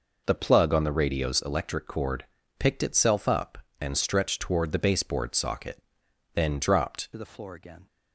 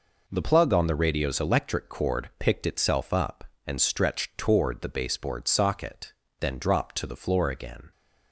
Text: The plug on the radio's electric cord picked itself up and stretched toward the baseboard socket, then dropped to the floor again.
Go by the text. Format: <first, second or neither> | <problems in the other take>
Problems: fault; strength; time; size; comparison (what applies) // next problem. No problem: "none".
second | pauses between "cord" and "picked"; slight; at 2.2 s; 0.34 s long // changes voice at "to"; from 7.1 s on; 0.7 s long